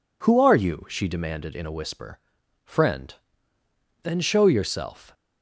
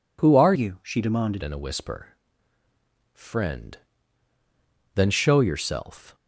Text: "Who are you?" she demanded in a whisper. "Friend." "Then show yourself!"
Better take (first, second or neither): first